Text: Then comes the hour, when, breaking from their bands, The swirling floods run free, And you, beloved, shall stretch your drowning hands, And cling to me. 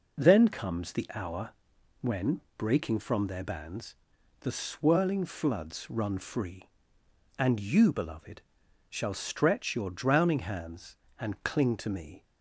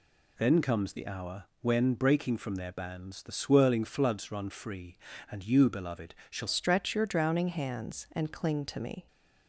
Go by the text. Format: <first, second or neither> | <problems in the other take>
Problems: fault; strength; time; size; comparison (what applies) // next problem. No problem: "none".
first | changes voice at "stretch"; from 6.4 s on; 2.6 s long